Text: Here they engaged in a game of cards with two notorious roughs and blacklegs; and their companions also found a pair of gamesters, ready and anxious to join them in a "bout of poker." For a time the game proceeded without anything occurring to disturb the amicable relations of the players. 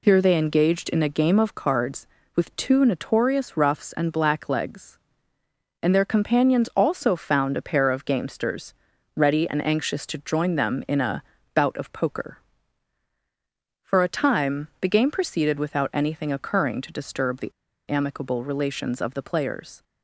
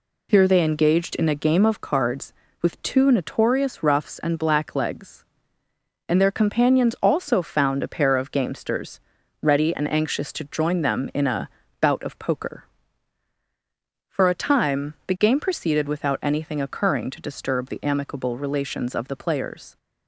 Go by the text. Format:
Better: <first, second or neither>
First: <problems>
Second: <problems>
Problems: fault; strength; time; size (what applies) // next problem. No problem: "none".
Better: second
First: pauses between "a" and "bout"; slight; at 11.2 s; 0.32 s long // pauses between "the" and "amicable"; at 17.4 s; 0.39 s long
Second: pauses between "a" and "bout"; slight; at 11.4 s; 0.32 s long